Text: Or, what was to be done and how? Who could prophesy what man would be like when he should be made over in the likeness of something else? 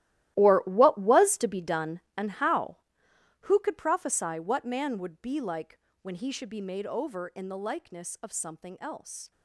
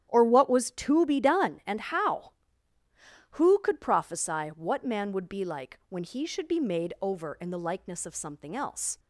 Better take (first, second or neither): second